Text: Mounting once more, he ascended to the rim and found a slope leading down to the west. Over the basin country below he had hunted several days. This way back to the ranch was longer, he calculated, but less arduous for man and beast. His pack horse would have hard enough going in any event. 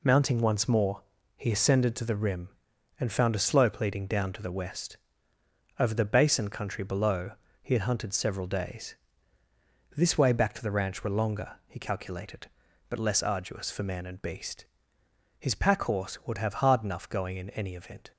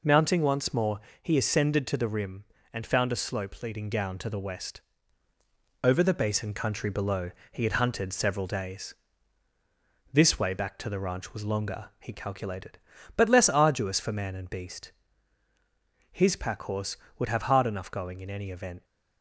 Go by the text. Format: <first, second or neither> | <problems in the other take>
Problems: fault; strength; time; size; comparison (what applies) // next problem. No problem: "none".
second | pauses between "below" and "he"; slight; at 7.3 s; 0.30 s long; slight in the second // says "were" for "was"; at 11.0 s